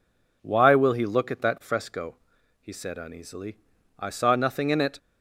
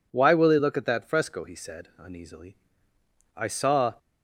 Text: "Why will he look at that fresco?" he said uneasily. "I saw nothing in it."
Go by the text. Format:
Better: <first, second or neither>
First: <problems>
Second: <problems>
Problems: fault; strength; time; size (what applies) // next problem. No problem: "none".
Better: first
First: none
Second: stops before "nothing in it"; at 3.9 s